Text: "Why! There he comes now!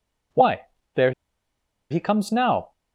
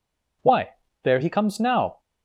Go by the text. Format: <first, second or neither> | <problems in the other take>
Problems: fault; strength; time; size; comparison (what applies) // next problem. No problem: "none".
second | pauses between "There" and "he"; noticeable; at 1.1 s; 0.79 s long